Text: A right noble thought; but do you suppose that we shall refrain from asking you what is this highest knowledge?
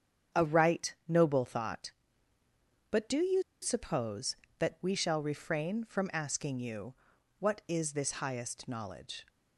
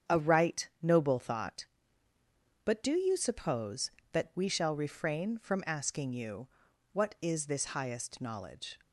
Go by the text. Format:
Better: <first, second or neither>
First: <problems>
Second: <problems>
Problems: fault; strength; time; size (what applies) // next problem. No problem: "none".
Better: second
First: starts louder than the rest; strong; until 1.4 s; 8 dB // pauses between "you" and "suppose"; slight; at 3.4 s; 0.19 s long // pauses between "you" and "what"; noticeable; at 6.9 s; 0.46 s long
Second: starts louder than the rest; strong; until 1.2 s; 8 dB // pauses between "you" and "what"; noticeable; at 6.4 s; 0.46 s long